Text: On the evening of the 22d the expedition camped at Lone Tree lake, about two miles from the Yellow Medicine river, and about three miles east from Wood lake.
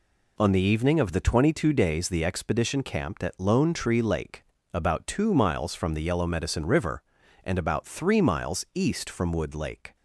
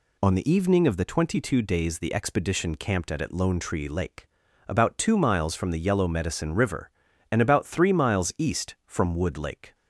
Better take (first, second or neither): first